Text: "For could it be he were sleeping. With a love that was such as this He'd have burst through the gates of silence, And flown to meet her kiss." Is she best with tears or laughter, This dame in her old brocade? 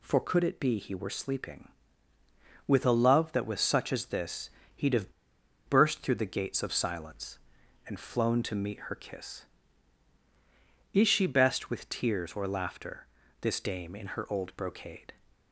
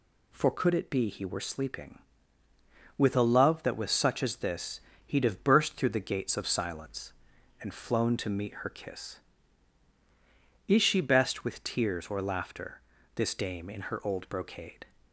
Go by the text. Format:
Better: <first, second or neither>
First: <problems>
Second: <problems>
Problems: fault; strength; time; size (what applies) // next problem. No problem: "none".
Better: second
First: pauses between "this" and "He'd"; slight; at 4.5 s; 0.24 s long // pauses between "have" and "burst"; noticeable; at 5.1 s; 0.56 s long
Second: pauses between "this" and "He'd"; slight; at 4.8 s; 0.24 s long